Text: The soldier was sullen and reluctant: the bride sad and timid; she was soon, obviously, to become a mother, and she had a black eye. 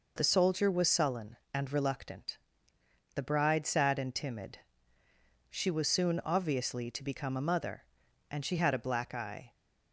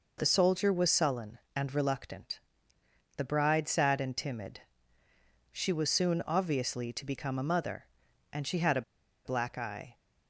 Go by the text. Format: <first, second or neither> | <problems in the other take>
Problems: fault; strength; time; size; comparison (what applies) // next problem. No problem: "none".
first | pauses between "a" and "black"; at 8.8 s; 0.43 s long